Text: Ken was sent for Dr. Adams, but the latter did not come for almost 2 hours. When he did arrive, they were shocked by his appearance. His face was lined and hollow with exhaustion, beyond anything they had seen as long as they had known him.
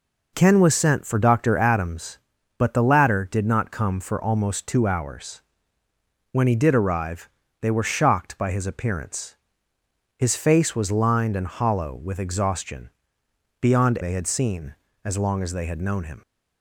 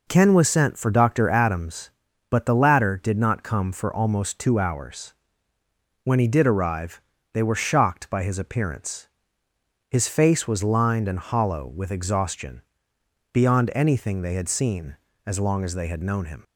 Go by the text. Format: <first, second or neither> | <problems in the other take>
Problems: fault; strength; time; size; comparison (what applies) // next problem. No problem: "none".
second | skips "anything"; at 14.0 s